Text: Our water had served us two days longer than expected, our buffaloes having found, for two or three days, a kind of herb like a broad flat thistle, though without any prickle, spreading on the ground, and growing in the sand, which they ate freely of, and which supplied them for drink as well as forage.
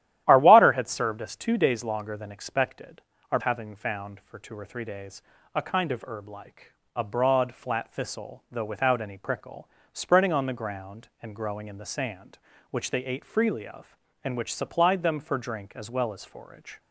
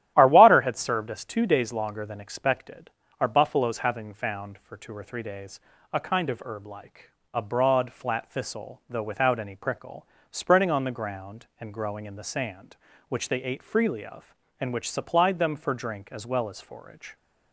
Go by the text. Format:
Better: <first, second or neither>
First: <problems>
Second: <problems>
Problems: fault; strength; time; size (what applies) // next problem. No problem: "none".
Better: second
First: starts louder than the rest; strong; until 1.2 s; 12.5 dB // skips "buffaloes"; at 3.3 s // pauses between "like" and "a"; slight; at 6.7 s; 0.26 s long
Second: starts louder than the rest; strong; until 1.1 s; 13 dB // pauses between "like" and "a"; slight; at 7.0 s; 0.26 s long